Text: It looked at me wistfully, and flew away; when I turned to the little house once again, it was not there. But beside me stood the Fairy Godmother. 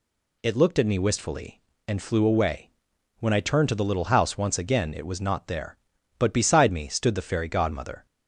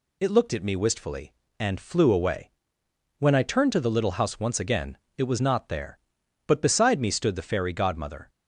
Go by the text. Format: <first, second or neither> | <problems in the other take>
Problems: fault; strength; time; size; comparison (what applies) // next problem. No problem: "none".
neither | none